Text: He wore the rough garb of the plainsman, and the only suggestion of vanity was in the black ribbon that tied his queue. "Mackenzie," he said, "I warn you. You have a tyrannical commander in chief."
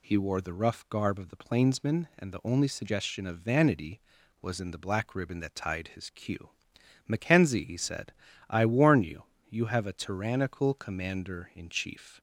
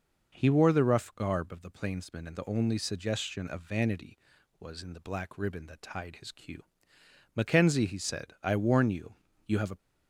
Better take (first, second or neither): first